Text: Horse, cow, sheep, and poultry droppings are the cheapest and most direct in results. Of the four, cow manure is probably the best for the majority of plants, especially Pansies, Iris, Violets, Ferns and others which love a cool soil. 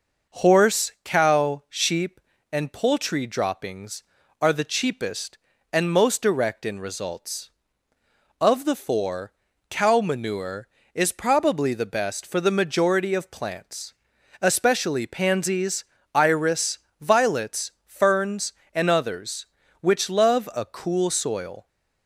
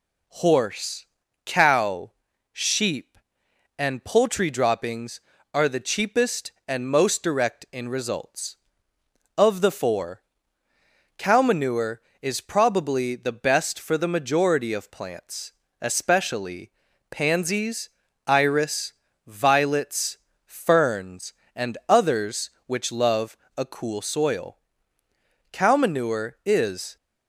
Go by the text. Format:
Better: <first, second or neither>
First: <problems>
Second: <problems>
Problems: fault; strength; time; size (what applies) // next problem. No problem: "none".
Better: first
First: none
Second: pauses between "especially" and "Pansies"; at 16.7 s; 0.40 s long // pauses between "love" and "a"; slight; at 23.3 s; 0.20 s long // goes on to say "Cow manure is"; from 25.5 s on; 1.4 s long